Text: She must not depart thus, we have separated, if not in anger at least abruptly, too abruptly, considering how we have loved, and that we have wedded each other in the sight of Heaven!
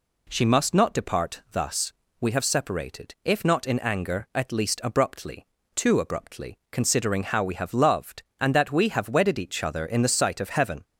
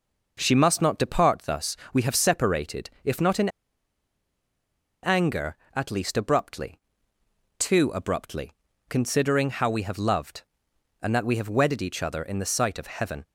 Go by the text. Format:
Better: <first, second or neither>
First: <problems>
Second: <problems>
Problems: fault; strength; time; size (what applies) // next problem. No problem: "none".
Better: first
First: none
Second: pauses between "in" and "anger"; strong; at 3.4 s; 1.5 s long